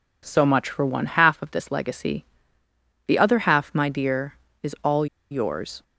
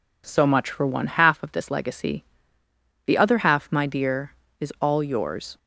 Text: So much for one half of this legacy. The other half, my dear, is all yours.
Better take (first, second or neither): second